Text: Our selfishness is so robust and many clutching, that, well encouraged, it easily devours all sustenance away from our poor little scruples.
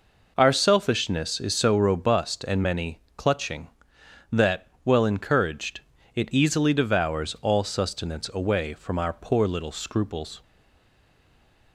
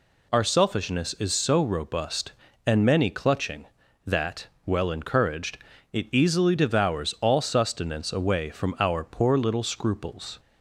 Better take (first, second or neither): second